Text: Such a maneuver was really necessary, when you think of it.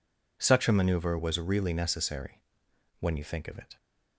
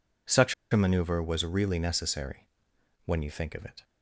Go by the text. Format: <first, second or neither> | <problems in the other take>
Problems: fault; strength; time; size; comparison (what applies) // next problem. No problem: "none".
first | pauses between "Such" and "a"; slight; at 0.5 s; 0.17 s long